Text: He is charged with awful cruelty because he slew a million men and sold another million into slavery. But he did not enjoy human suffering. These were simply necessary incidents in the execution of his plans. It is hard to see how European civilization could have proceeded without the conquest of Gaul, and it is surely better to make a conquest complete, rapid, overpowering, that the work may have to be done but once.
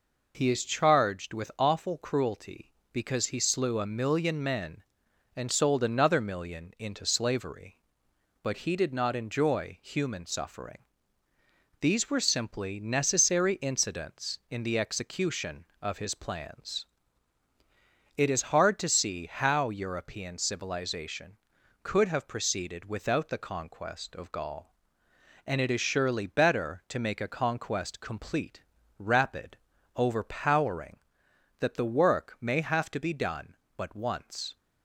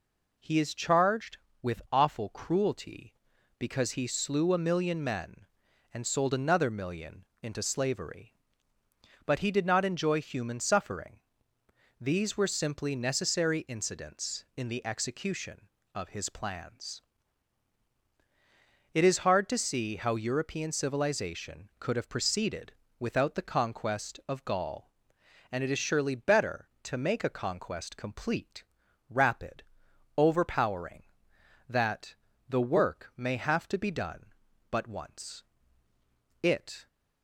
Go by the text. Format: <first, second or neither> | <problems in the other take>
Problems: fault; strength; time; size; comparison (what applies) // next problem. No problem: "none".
first | pauses between "million" and "into"; slight; at 7.2 s; 0.18 s long // pauses between "proceeded" and "without"; slight; at 22.7 s; 0.28 s long // pauses between "that" and "the"; slight; at 32.1 s; 0.35 s long // goes on to say "It"; slight; from 36.4 s on; 0.44 s long